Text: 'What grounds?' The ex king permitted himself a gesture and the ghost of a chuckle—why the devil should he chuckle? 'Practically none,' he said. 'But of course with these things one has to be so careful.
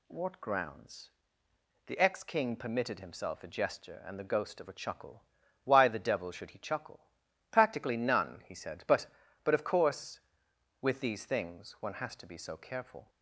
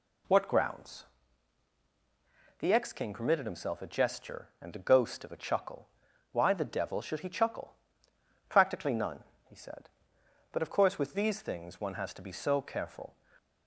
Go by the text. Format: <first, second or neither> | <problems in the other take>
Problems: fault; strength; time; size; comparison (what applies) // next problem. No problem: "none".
second | says "But" twice; at 9.4 s